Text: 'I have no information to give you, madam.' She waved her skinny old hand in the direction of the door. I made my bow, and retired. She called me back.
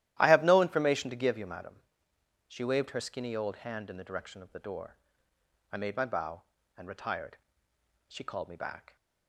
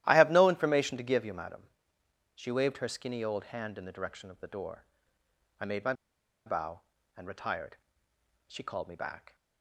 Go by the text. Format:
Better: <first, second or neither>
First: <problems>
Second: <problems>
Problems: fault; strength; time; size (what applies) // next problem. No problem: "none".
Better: first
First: starts louder than the rest; strong; until 1.2 s; 13.5 dB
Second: starts louder than the rest; strong; until 1.0 s; 13.5 dB // pauses between "my" and "bow"; noticeable; at 5.9 s; 0.53 s long